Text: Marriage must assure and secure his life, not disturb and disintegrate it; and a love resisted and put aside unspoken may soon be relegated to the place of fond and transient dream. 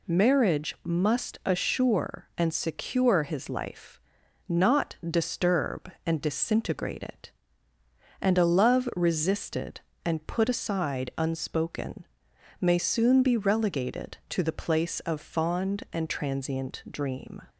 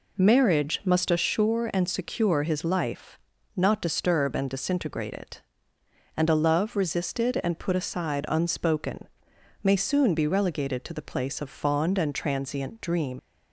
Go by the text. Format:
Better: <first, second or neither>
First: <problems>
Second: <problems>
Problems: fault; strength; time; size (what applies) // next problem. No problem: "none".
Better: first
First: pauses between "unspoken" and "may"; noticeable; at 12.0 s; 0.54 s long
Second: pauses between "unspoken" and "may"; noticeable; at 9.0 s; 0.53 s long // leaves "dream" unfinished; at 13.1 s; 105 ms